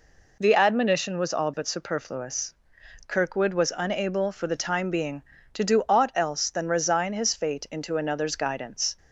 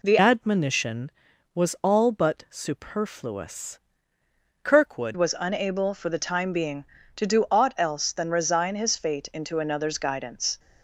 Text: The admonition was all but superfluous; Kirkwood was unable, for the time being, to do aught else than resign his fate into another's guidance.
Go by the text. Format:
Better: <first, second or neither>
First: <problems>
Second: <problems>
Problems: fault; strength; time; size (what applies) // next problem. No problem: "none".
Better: first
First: none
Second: changes voice from "admonition" to "Kirkwood"; from 0.1 to 5.1 s; 5.0 s long